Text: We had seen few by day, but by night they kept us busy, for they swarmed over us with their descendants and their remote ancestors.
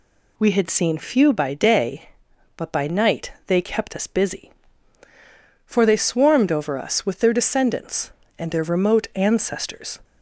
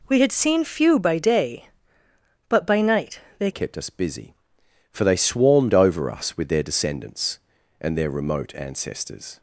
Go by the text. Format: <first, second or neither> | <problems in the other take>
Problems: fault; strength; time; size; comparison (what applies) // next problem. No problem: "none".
first | pauses between "night" and "they"; slight; at 3.2 s; 0.18 s long // changes voice at "kept"; from 3.5 s on; 5.8 s long